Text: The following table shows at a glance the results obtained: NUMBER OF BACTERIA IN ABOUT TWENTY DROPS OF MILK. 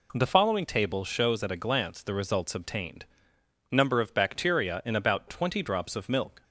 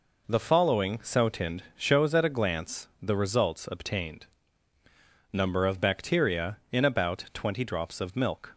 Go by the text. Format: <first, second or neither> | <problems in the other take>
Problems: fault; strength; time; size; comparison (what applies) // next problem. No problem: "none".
first | says "sotind" for "table"; at 1.0 s